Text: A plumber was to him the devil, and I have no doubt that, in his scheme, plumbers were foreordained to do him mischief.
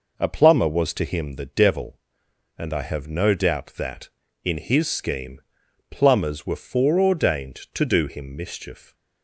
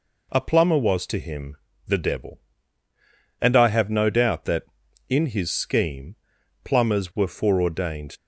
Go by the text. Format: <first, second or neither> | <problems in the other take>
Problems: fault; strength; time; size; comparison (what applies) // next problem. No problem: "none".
first | pauses between "him" and "the"; slight; at 1.5 s; 0.30 s long // stops before "to do him mischief"; at 8.1 s